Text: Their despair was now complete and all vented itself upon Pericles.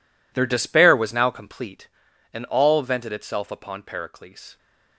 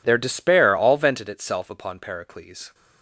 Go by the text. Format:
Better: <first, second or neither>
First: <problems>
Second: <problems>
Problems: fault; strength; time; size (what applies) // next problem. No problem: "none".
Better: first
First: none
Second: skips "was now complete and"; at 0.7 s